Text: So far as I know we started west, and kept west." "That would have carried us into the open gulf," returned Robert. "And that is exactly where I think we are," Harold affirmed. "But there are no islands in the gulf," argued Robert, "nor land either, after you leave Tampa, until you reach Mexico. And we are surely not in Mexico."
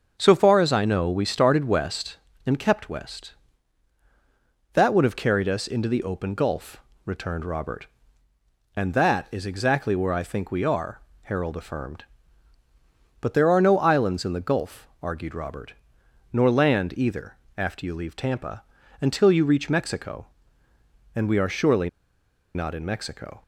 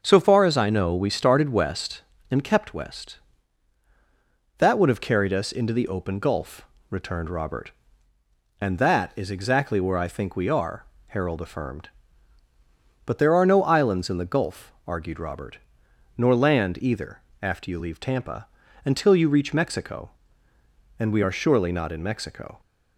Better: second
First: starts louder than the rest; noticeable; until 1.1 s; 6 dB // pauses between "surely" and "not"; noticeable; at 21.8 s; 0.66 s long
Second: starts louder than the rest; until 1.0 s; 6.5 dB

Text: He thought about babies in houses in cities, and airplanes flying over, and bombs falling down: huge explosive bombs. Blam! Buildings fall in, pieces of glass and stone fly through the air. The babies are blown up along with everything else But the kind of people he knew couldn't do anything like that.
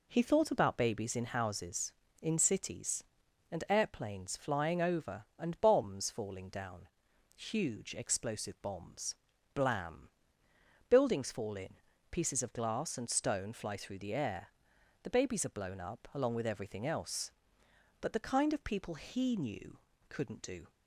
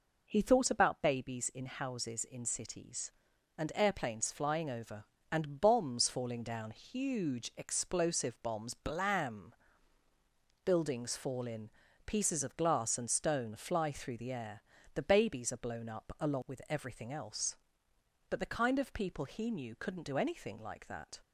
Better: second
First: pauses between "knew" and "couldn't"; slight; at 19.7 s; 0.30 s long // stops before "anything like that"; at 20.6 s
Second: none

